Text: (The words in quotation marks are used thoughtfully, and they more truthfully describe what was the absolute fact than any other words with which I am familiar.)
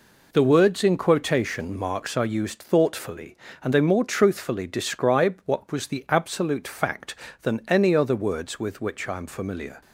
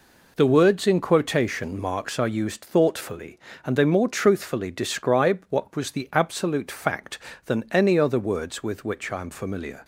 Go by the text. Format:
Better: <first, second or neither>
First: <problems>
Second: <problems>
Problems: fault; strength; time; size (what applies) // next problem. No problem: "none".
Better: neither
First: none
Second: none